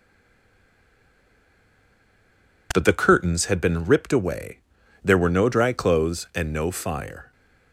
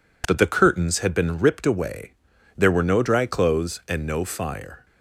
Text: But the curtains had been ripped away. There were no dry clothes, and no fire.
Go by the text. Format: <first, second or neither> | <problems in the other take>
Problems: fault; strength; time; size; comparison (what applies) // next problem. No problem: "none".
second | stays silent before the first word; strong; until 2.7 s; 2.7 s long